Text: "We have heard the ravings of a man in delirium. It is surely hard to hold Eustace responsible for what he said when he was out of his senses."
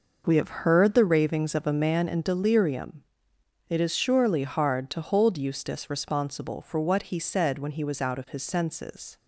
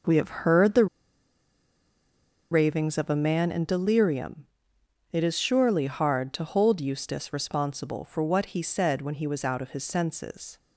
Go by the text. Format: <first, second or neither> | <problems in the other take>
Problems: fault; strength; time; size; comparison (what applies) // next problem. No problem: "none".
first | pauses between "the" and "ravings"; strong; at 0.8 s; 1.6 s long